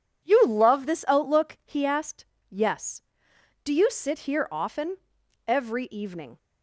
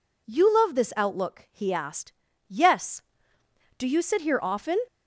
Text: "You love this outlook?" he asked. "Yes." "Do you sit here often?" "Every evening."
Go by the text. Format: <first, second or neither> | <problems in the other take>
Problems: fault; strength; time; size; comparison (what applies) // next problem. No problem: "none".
first | stops before "Every evening"; at 4.8 s